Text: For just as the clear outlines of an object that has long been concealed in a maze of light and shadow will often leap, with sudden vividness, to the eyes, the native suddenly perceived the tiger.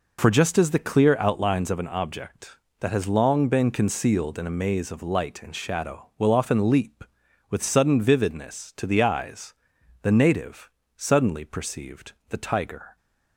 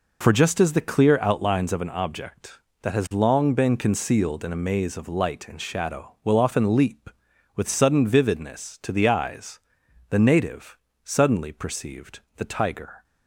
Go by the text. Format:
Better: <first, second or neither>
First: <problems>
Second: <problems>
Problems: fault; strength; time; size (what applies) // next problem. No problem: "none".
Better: neither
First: pauses between "native" and "suddenly"; slight; at 10.6 s; 0.26 s long // pauses between "perceived" and "the"; slight; at 12.1 s; 0.16 s long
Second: pauses between "native" and "suddenly"; slight; at 10.7 s; 0.26 s long // pauses between "perceived" and "the"; slight; at 12.2 s; 0.16 s long